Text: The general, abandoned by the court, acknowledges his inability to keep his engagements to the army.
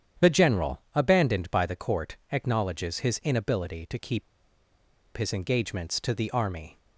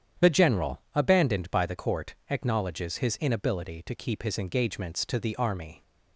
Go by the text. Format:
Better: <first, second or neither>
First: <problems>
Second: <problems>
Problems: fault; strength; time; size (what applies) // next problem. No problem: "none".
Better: second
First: starts louder than the rest; strong; until 1.3 s; 9 dB // pauses between "keep" and "his"; noticeable; at 4.2 s; 0.93 s long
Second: starts louder than the rest; strong; until 1.3 s; 9 dB